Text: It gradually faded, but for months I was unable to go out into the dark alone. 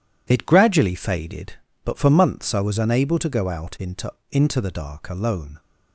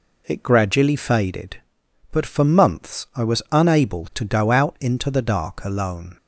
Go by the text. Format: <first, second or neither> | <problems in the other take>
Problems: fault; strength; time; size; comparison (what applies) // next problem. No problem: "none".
second | says "into" twice; at 4.2 s